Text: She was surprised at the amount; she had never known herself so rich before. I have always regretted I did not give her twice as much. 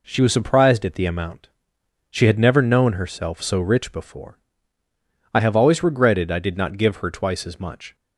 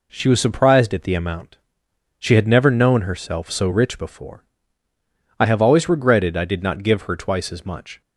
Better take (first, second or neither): neither